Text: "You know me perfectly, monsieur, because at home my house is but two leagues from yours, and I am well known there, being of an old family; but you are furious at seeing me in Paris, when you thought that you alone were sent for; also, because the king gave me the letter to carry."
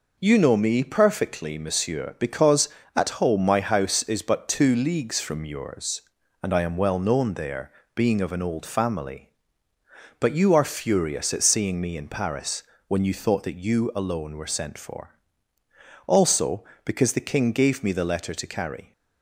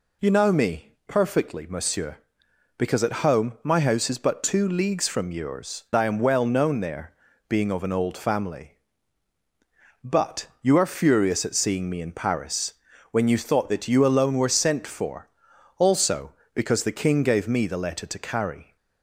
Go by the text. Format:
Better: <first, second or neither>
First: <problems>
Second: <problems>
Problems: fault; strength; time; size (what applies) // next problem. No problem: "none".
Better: first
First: none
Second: skips "and"; at 5.9 s